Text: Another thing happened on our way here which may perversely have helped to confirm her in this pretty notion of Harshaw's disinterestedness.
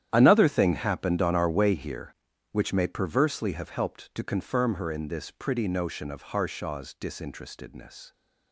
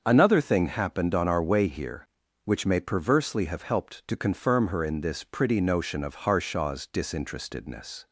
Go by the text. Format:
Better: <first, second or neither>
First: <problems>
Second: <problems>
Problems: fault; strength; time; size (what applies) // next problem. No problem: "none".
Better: second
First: gets quieter; strong; throughout; 14.5 dB // starts louder than the rest; strong; until 1.1 s; 10.5 dB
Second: starts louder than the rest; until 1.0 s; 6.5 dB